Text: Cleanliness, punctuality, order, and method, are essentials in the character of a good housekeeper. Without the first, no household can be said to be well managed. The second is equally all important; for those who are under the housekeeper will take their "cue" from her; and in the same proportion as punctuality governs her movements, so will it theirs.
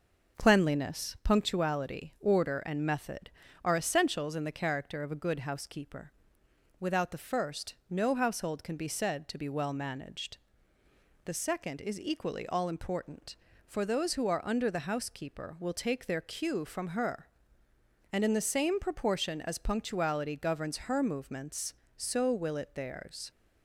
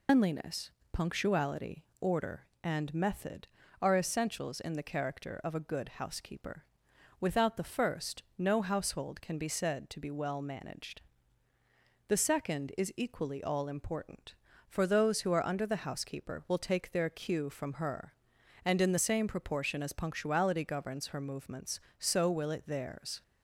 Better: first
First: none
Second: loses the start of "Cleanliness"; at 0.0 s; 165 ms

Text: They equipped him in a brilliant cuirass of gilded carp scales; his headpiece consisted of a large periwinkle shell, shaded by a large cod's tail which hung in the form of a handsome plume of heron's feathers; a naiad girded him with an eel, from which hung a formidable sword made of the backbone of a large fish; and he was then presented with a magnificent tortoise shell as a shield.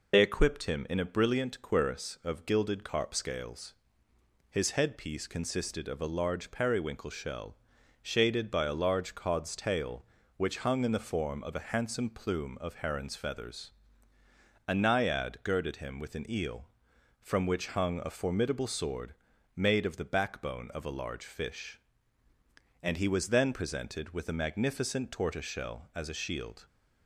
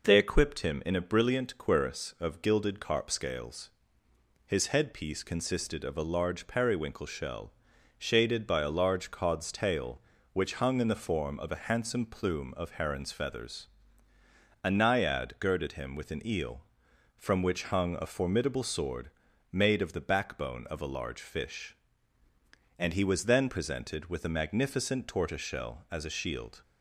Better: second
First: loses the start of "They"; at 0.1 s; 50 ms // pauses between "sword" and "made"; at 19.1 s; 0.42 s long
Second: pauses between "sword" and "made"; at 19.0 s; 0.42 s long

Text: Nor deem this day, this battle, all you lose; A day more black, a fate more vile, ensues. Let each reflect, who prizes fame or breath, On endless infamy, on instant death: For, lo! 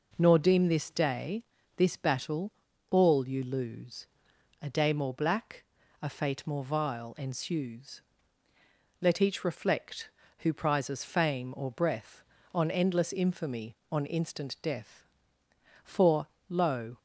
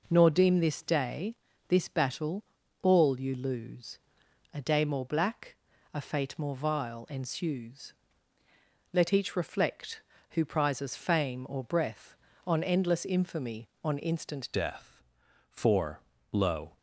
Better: first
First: none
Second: changes voice at "death"; from 14.5 s on; 2.2 s long

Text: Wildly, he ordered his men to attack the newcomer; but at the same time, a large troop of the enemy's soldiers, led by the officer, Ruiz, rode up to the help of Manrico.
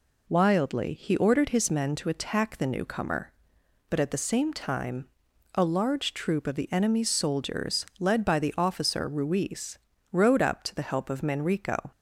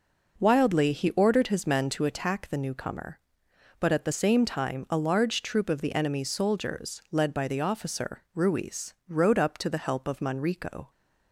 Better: neither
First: none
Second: none

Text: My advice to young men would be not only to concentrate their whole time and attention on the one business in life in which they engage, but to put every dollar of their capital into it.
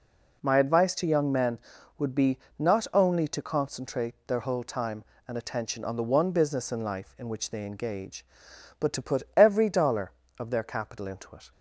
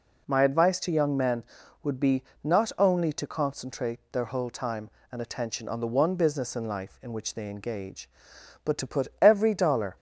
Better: first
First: pauses between "be" and "not"; slight; at 2.3 s; 0.20 s long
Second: pauses between "be" and "not"; slight; at 2.2 s; 0.20 s long // stops before "of their capital into it"; at 9.9 s

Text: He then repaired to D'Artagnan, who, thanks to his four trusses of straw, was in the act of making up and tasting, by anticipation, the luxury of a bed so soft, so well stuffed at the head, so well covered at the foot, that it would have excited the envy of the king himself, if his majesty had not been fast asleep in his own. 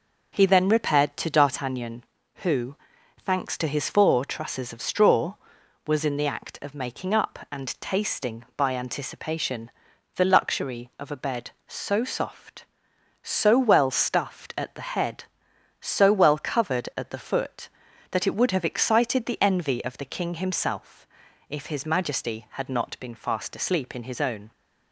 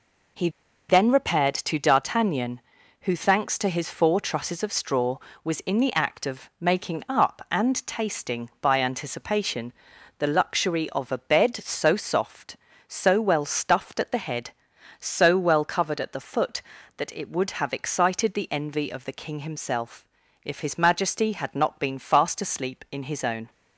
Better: first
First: none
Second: pauses between "He" and "then"; at 0.4 s; 0.40 s long

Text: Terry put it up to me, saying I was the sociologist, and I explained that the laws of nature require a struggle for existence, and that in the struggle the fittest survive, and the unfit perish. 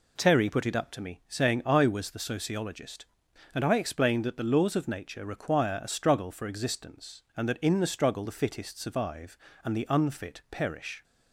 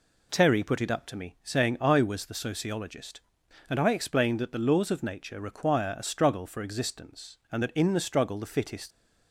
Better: first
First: none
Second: stops before "survive and the unfit perish"; at 8.9 s

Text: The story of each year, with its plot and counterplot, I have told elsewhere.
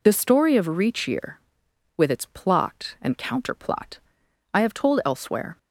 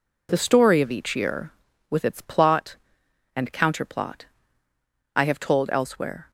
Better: second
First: says "reach" for "each"; at 0.6 s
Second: none

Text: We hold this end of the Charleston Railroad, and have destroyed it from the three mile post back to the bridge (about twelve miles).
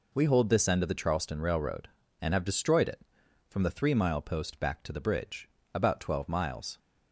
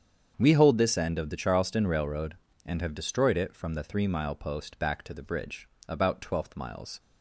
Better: first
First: none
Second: starts louder than the rest; strong; until 1.3 s; 7.5 dB // says "twelfth" for "twelve"; at 6.2 s

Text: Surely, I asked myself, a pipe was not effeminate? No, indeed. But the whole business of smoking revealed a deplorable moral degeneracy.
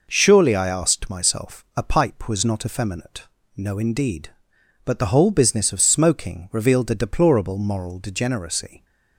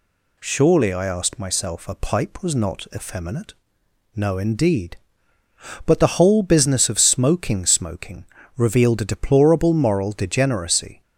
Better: first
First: none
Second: says "smoking" twice; at 7.6 s

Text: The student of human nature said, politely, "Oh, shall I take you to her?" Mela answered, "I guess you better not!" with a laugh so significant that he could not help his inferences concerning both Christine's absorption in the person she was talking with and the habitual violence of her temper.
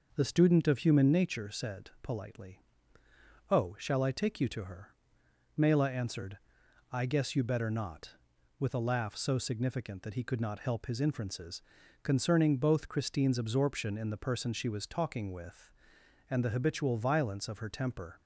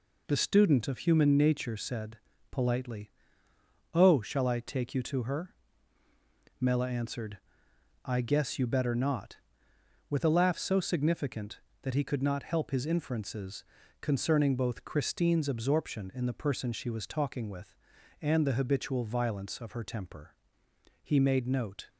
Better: first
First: pauses between "inferences" and "concerning"; at 11.6 s; 0.40 s long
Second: pauses between "inferences" and "concerning"; at 13.6 s; 0.38 s long // goes on to say "He made note"; noticeable; from 21.0 s on; 0.86 s long

